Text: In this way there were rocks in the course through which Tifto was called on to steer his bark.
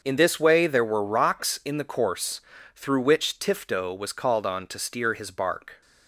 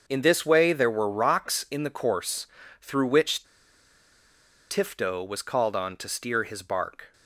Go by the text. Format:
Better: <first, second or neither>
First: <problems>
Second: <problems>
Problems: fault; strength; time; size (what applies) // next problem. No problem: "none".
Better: first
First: starts louder than the rest; until 1.0 s; 6.5 dB // pauses between "course" and "through"; slight; at 2.4 s; 0.34 s long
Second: starts louder than the rest; until 1.0 s; 6.5 dB // pauses between "course" and "through"; slight; at 2.4 s; 0.34 s long // pauses between "which" and "Tifto"; strong; at 3.4 s; 1.2 s long